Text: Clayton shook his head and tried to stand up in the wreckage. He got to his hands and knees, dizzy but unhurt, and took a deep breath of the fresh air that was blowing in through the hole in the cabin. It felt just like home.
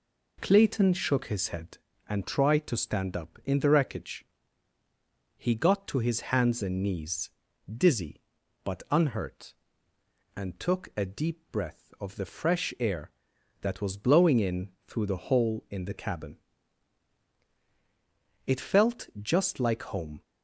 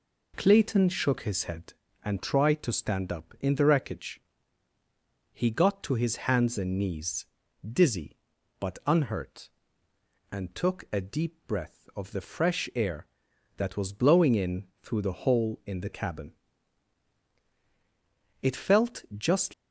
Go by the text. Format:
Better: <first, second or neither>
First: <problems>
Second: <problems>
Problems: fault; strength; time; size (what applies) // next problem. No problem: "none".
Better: first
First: pauses between "in" and "through"; slight; at 14.6 s; 0.18 s long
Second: pauses between "in" and "through"; slight; at 14.6 s; 0.18 s long // stops before "like home"; at 19.5 s